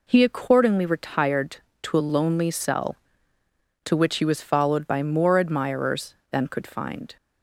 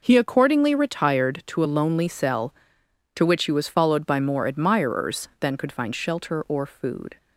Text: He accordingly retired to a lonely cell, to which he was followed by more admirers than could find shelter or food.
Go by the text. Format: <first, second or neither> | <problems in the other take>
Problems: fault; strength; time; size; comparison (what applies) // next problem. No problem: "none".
second | stops before "shelter or food"; at 7.1 s